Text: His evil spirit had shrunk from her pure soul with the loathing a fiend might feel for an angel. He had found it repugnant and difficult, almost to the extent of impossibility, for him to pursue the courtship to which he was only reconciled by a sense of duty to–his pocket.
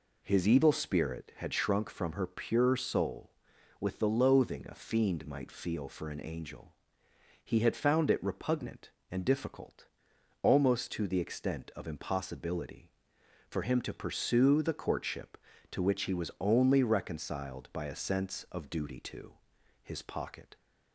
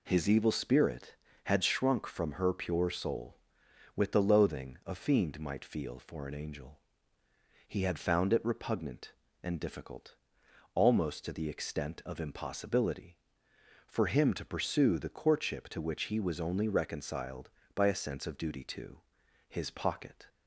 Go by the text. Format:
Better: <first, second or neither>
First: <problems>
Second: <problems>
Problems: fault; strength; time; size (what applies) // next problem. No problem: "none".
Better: neither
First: none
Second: none